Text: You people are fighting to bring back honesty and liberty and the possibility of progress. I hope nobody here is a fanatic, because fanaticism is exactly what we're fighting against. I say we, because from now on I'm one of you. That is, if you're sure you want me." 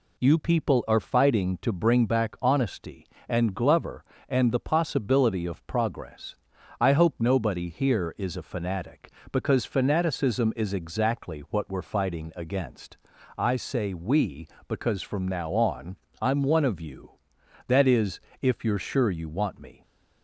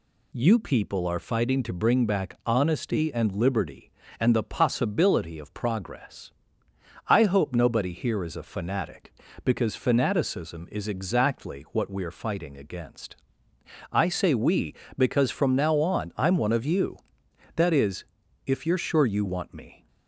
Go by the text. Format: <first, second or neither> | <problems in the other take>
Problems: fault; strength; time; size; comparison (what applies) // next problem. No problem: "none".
second | says "glover" for "liberty"; at 3.5 s // pauses between "on" and "I'm"; slight; at 15.9 s; 0.24 s long